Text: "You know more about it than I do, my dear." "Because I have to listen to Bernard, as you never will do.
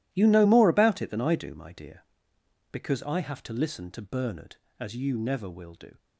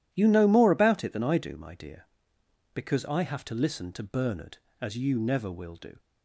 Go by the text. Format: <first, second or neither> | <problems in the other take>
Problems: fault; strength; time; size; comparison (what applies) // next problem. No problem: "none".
second | gets quieter; strong; throughout; 14.5 dB